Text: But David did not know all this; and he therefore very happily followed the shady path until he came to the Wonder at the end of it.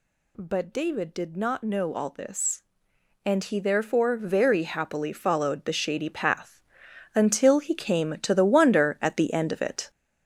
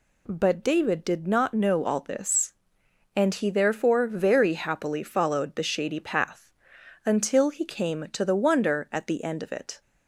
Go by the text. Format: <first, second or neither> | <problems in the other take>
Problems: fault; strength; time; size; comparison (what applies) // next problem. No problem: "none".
second | gets louder; noticeable; throughout; 6 dB // pauses between "path" and "until"; noticeable; at 6.5 s; 0.54 s long; noticeable in the second